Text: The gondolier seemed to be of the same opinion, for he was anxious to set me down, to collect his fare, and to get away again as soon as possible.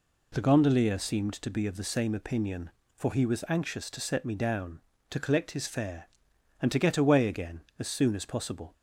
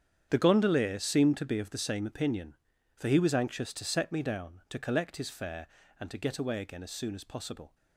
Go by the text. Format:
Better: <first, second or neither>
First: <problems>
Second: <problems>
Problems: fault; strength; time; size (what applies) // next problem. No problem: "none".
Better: first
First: none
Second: gets quieter; strong; throughout; 14 dB